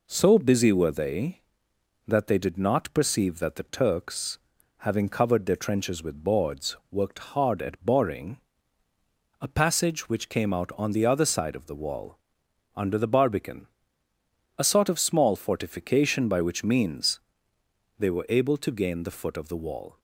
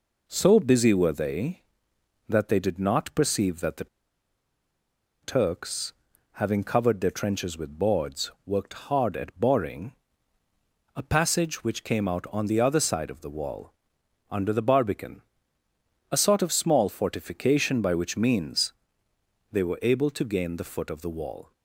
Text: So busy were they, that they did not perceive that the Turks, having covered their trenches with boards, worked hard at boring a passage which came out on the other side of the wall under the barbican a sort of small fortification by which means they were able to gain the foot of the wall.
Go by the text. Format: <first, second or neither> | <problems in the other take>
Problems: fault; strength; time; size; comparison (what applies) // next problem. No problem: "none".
first | pauses between "the" and "Turks"; strong; at 3.8 s; 1.3 s long // pauses between "boring" and "a"; at 9.9 s; 1.0 s long; also in the first // pauses between "wall" and "under"; noticeable; at 13.7 s; 0.56 s long; noticeable in the first // pauses between "barbican" and "a"; noticeable; at 15.2 s; 0.88 s long; noticeable in the first // pauses between "means" and "they"; noticeable; at 18.7 s; 0.80 s long; noticeable in the first